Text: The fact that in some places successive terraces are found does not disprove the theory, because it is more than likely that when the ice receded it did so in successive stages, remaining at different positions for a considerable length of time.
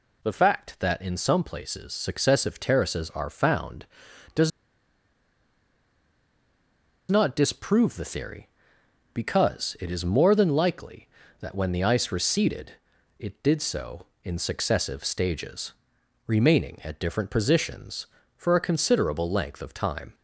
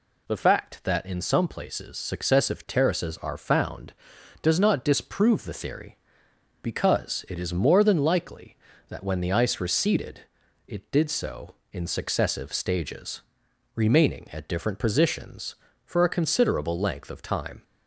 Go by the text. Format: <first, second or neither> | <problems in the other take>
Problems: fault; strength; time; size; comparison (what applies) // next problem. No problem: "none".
second | pauses between "does" and "not"; strong; at 4.5 s; 2.6 s long // pauses between "receded" and "it"; noticeable; at 12.7 s; 0.46 s long; noticeable in the second